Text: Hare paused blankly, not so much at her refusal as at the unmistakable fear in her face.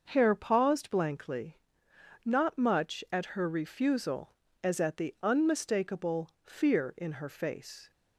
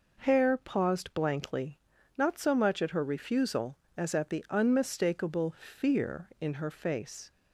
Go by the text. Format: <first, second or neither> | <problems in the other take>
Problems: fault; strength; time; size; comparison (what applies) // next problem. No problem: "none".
second | starts louder than the rest; until 1.1 s; 6 dB // skips "so"; at 2.5 s